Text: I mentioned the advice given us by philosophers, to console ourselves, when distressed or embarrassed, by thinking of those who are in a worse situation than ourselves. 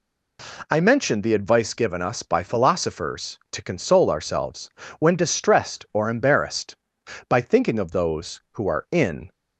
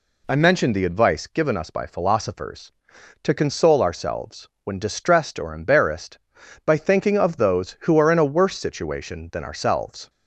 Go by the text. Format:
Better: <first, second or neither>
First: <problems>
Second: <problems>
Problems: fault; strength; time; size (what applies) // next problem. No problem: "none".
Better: second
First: stops before "a worse situation than ourselves"; at 9.3 s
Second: none